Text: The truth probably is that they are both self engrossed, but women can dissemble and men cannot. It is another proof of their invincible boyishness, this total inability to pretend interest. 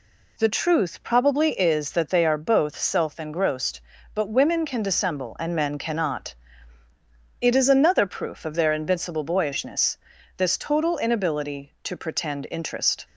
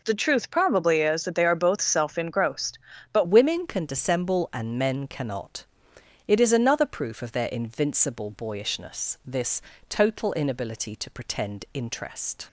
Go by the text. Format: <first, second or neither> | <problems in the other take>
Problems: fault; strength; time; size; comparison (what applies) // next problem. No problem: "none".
first | changes voice at "women"; from 3.2 s on; 9.2 s long // pauses between "this" and "total"; slight; at 9.6 s; 0.28 s long